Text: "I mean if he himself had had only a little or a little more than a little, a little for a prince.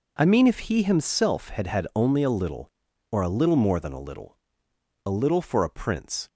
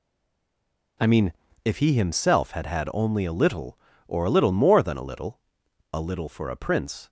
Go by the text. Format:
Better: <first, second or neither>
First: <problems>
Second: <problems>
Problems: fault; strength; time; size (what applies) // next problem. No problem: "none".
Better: first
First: none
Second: stays silent before the first word; until 0.9 s; 0.9 s long // pauses between "mean" and "if"; slight; at 1.3 s; 0.32 s long